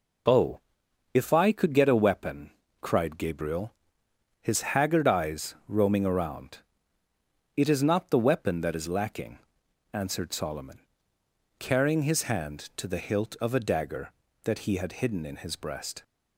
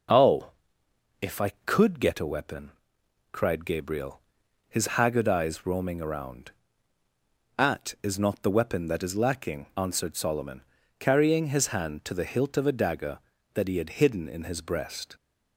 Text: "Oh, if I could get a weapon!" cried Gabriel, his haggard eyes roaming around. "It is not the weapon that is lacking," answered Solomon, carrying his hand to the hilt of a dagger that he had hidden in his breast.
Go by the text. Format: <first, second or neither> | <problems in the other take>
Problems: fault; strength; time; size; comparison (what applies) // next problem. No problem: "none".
first | says "At" for "It"; at 7.5 s